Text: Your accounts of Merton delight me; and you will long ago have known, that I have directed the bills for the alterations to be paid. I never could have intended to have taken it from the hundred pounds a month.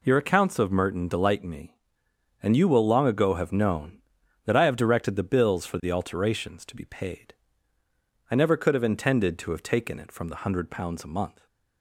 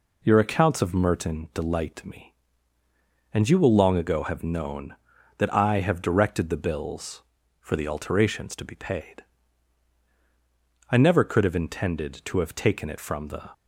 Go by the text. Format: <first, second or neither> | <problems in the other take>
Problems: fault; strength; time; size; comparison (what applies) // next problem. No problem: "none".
first | stops before "hundred pounds a month"; at 13.5 s